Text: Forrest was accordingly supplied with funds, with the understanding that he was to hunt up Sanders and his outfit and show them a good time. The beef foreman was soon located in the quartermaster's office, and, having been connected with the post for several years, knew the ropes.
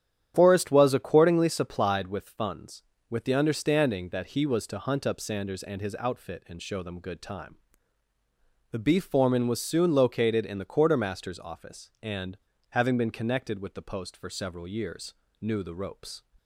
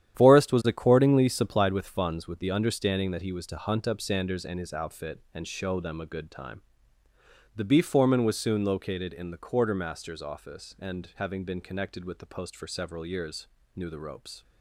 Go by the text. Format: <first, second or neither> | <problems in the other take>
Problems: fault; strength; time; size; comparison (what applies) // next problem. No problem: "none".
second | starts louder than the rest; strong; until 1.3 s; 10 dB; strong in the second // skips "a"; at 6.9 s